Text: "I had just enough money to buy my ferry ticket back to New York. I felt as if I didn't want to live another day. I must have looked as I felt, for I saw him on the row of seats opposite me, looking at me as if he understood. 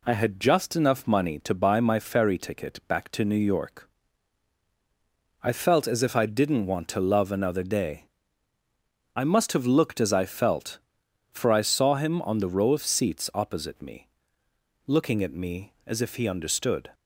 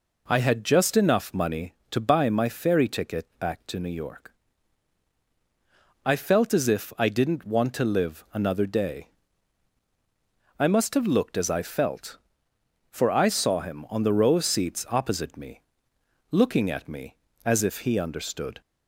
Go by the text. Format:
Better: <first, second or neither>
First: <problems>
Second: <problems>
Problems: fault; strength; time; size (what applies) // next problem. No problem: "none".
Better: second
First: says "love" for "live"; at 6.9 s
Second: none